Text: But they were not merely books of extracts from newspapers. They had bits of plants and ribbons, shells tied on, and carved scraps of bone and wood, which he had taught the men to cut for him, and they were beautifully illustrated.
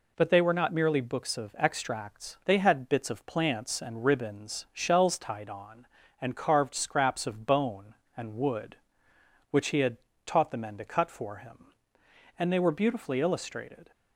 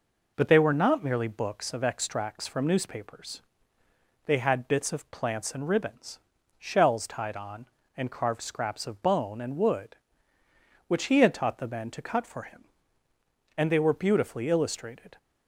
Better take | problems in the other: second | skips "from newspapers"; at 2.4 s // pauses between "had" and "taught"; slight; at 9.9 s; 0.28 s long

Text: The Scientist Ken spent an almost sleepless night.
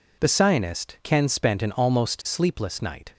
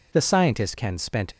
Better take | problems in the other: first | stops before "an almost sleepless night"; at 1.3 s

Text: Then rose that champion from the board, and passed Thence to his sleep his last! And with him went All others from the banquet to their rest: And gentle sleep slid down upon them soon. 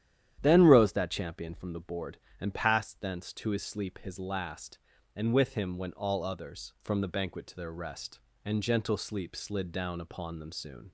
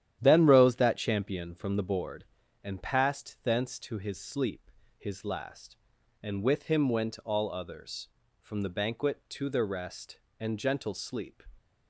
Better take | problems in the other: first | starts louder than the rest; strong; until 1.2 s; 11 dB; strong in the first // pauses between "sleep" and "his"; slight; at 4.6 s; 0.28 s long // stops before "slid down upon them soon"; at 11.5 s

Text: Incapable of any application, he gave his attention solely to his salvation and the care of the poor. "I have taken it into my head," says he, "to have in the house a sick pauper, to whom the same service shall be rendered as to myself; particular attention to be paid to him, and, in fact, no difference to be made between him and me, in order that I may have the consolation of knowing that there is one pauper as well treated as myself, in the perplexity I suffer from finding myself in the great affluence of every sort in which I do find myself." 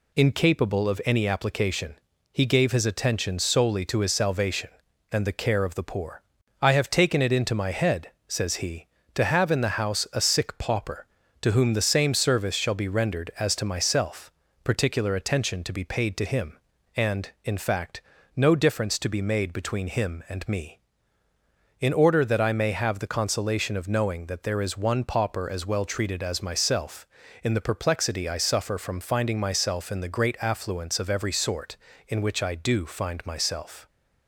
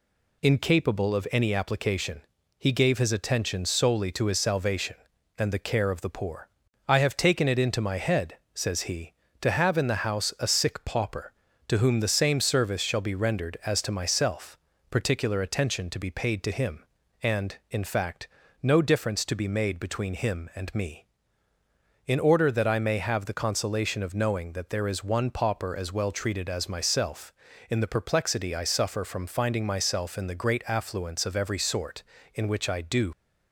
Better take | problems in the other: first | stops before "find myself"; at 33.1 s

